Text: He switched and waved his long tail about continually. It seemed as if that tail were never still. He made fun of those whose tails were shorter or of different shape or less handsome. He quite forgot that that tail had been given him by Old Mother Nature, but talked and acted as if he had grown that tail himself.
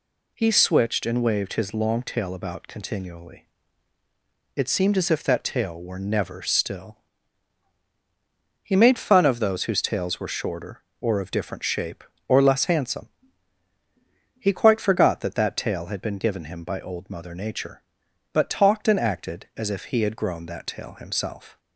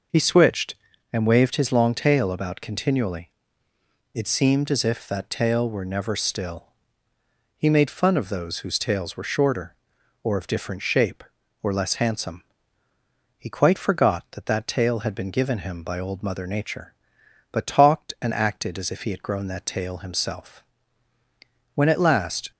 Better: first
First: none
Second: goes on to say "When at last"; noticeable; from 21.7 s on; 0.76 s long

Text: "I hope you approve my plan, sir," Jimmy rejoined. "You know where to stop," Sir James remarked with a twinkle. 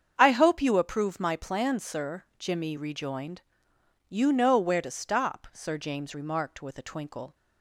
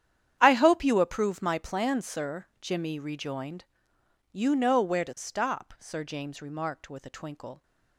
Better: first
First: starts louder than the rest; strong; until 1.1 s; 7.5 dB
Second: gets quieter; strong; throughout; 16 dB // starts louder than the rest; strong; until 1.4 s; 9.5 dB

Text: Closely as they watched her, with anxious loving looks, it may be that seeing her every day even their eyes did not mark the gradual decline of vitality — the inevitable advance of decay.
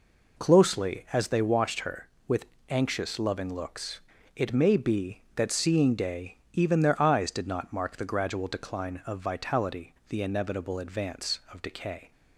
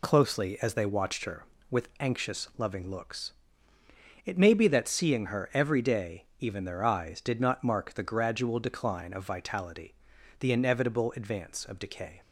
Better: second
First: pauses between "with" and "anxious"; slight; at 2.4 s; 0.24 s long // skips "her every"; at 5.9 s // pauses between "day" and "even"; slight; at 6.3 s; 0.16 s long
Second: none

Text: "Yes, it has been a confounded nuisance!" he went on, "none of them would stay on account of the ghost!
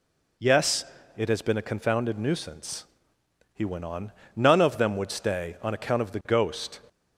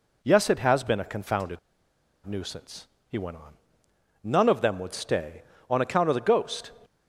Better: first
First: none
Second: pauses between "confounded" and "nuisance"; noticeable; at 1.5 s; 0.67 s long

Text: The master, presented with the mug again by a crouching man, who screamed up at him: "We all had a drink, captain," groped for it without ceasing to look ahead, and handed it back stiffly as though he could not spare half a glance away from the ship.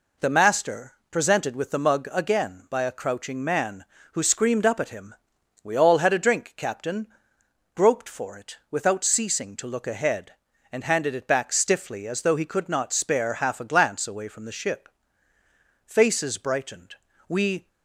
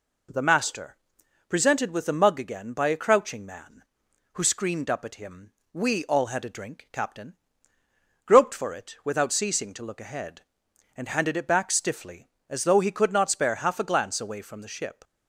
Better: second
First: goes on to say "Faces brightened We"; strong; from 15.8 s on; 1.8 s long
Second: none

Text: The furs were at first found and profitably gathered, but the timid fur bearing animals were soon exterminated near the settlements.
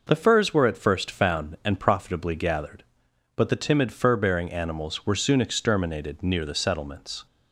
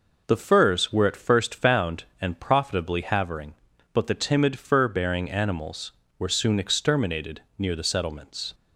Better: first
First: none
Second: says "havering" for "gathered"; at 3.0 s // pauses between "exterminated" and "near"; slight; at 7.4 s; 0.16 s long

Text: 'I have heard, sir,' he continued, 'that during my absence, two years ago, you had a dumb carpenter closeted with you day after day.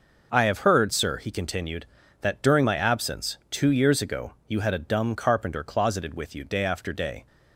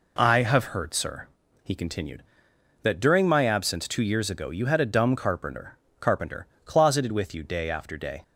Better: first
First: none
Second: says "carpenter" twice; at 5.9 s

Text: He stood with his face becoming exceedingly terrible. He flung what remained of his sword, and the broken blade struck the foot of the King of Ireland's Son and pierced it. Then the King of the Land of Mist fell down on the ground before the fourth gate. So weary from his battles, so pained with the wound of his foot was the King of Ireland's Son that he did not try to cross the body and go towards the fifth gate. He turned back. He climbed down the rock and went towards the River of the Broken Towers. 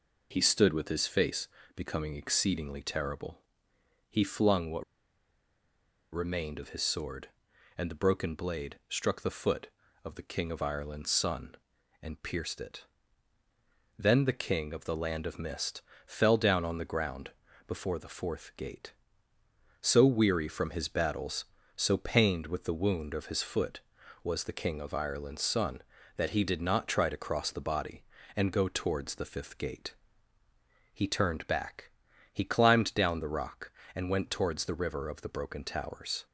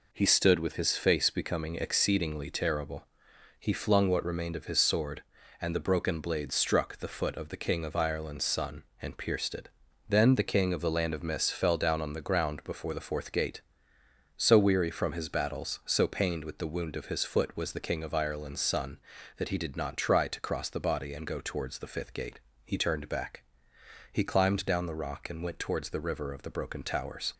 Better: second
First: pauses between "face" and "becoming"; slight; at 1.4 s; 0.26 s long // pauses between "what" and "remained"; strong; at 4.8 s; 1.2 s long // pauses between "Mist" and "fell"; slight; at 15.8 s; 0.24 s long // pauses between "ground" and "before"; slight; at 17.3 s; 0.36 s long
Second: none

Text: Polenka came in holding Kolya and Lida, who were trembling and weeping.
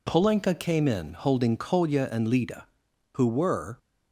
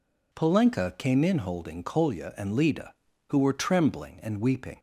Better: second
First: stops before "trembling and weeping"; at 3.7 s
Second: none

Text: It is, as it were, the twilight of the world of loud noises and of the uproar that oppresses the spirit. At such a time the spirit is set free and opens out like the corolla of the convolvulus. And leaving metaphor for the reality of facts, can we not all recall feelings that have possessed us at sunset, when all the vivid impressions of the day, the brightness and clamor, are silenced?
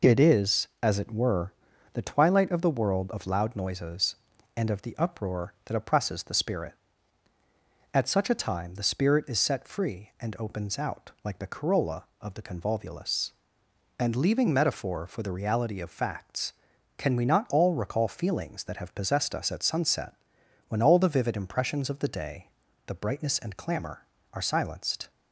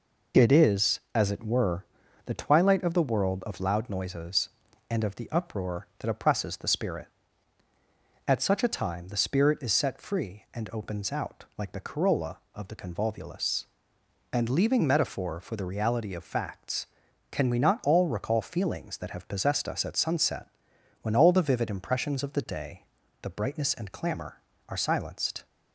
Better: neither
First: none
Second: none

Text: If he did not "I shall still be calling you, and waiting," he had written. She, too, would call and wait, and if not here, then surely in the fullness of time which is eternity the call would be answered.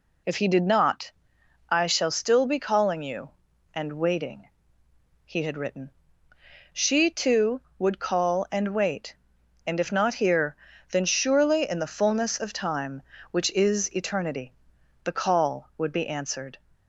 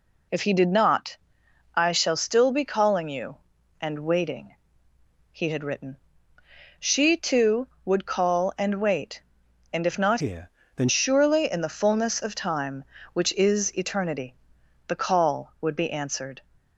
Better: first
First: pauses between "not" and "I"; noticeable; at 1.1 s; 0.58 s long // pauses between "eternity" and "the"; noticeable; at 14.5 s; 0.52 s long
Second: pauses between "not" and "I"; noticeable; at 1.1 s; 0.58 s long // changes voice from "here" to "then"; from 10.1 to 10.8 s; 0.7 s long // pauses between "eternity" and "the"; noticeable; at 14.3 s; 0.54 s long

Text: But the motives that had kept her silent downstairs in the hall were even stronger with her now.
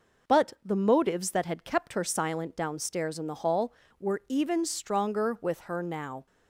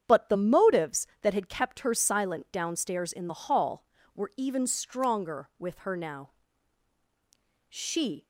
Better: first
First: none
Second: starts louder than the rest; strong; until 1.0 s; 8 dB // goes on to say "She"; from 7.6 s on; 0.58 s long

